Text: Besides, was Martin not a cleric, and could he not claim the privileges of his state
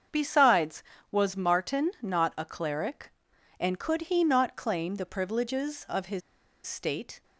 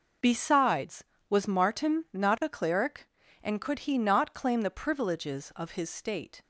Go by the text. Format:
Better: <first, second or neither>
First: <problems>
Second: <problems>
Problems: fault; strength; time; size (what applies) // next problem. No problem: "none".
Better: second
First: starts louder than the rest; until 1.4 s; 7 dB // pauses between "his" and "state"; noticeable; at 6.2 s; 0.46 s long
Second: none